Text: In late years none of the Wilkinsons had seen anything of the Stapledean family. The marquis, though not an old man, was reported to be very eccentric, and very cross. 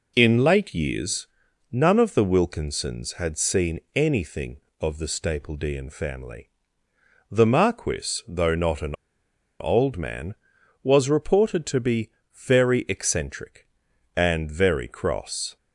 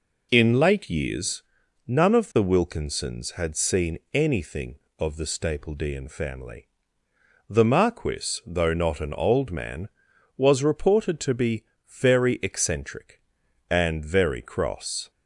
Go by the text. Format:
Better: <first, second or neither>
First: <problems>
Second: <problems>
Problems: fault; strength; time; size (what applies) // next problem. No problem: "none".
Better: second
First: pauses between "years" and "none"; noticeable; at 1.2 s; 0.46 s long // pauses between "seen" and "anything"; slight; at 3.7 s; 0.16 s long // pauses between "an" and "old"; noticeable; at 8.9 s; 0.66 s long // pauses between "be" and "very"; slight; at 12.1 s; 0.22 s long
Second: pauses between "years" and "none"; noticeable; at 1.4 s; 0.46 s long // pauses between "seen" and "anything"; slight; at 3.9 s; 0.16 s long // pauses between "be" and "very"; slight; at 11.6 s; 0.22 s long